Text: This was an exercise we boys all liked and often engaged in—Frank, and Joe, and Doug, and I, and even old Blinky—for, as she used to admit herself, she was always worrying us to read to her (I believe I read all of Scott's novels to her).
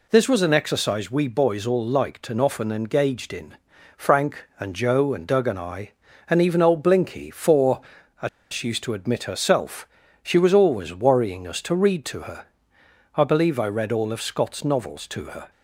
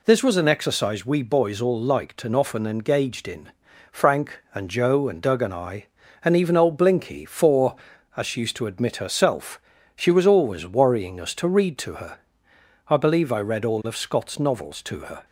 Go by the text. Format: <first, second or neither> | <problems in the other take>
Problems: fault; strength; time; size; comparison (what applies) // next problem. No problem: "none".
second | pauses between "as" and "she"; slight; at 8.2 s; 0.22 s long